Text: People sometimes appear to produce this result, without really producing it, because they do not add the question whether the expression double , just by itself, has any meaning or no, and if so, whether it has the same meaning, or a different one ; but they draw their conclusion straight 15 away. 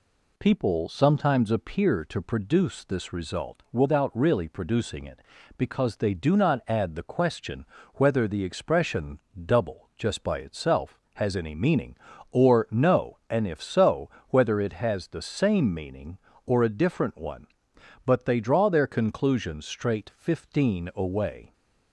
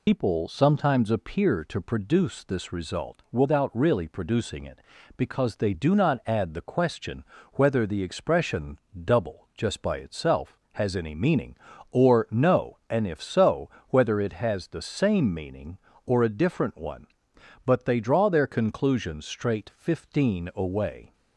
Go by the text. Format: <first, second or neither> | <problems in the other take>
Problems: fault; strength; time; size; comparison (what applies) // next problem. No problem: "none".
first | loses the start of "People"; at 0.0 s; 100 ms // pauses between "question" and "whether"; slight; at 7.2 s; 0.30 s long; slight in the first // pauses between "expression" and "double"; slight; at 8.7 s; 0.26 s long; slight in the first